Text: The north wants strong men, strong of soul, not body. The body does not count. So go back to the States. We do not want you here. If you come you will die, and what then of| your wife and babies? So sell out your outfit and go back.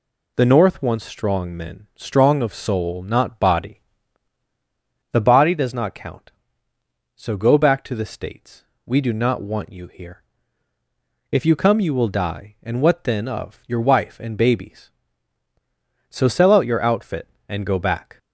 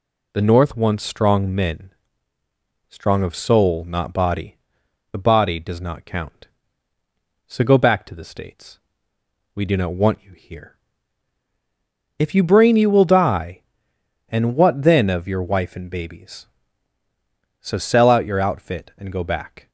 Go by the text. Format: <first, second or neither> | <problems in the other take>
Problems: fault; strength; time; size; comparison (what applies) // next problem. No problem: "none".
first | says "brain" for "come"; at 12.4 s